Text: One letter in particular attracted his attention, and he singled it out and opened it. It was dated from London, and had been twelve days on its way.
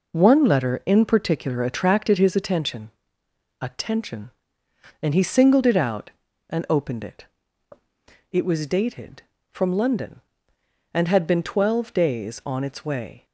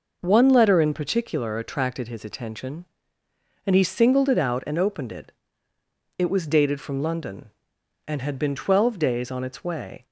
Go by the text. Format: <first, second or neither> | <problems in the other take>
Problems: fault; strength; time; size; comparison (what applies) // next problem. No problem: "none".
second | says "attention" twice; at 3.6 s